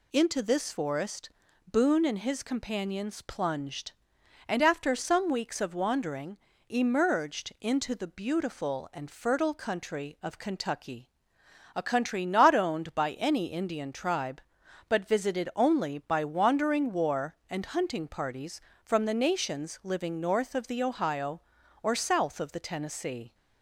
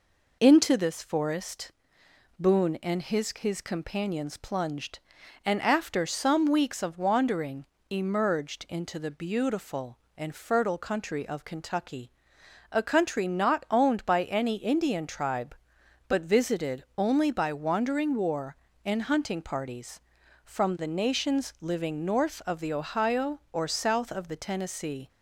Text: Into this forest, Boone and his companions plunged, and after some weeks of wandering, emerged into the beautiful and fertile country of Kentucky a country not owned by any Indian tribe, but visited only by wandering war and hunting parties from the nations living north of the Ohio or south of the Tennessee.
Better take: first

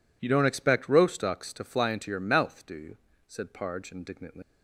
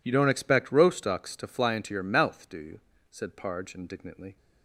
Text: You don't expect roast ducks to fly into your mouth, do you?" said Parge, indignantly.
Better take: second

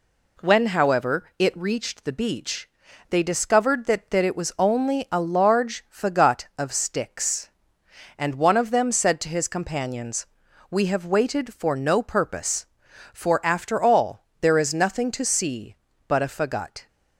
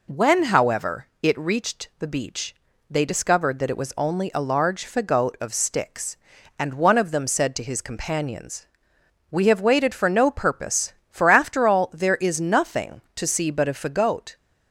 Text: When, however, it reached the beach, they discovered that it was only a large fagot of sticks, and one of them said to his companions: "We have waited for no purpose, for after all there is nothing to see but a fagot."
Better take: second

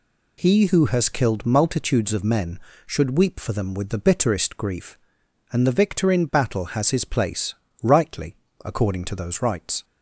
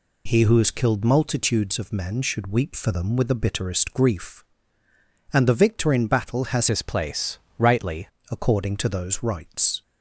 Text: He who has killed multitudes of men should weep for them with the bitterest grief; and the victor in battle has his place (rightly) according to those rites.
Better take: first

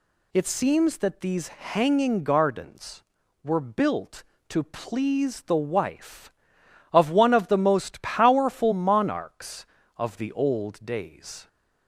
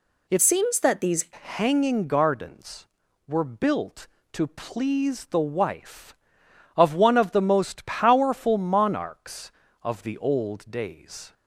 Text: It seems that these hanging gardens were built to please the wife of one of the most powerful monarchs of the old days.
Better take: first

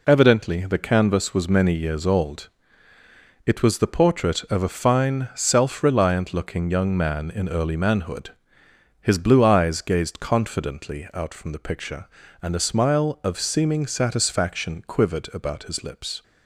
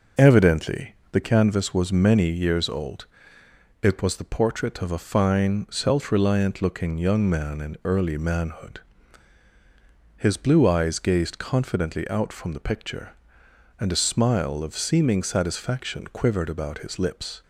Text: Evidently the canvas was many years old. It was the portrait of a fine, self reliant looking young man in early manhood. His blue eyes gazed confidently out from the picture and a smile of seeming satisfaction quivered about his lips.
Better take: first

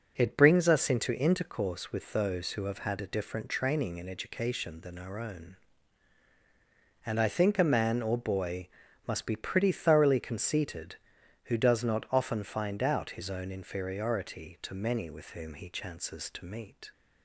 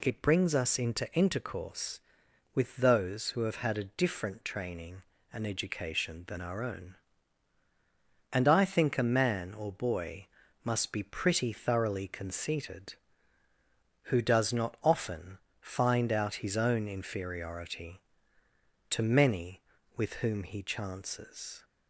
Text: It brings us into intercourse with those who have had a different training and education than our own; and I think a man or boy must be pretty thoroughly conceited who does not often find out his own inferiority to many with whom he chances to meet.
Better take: first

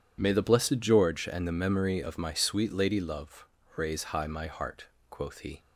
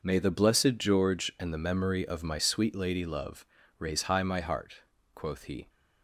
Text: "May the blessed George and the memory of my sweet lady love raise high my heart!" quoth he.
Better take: neither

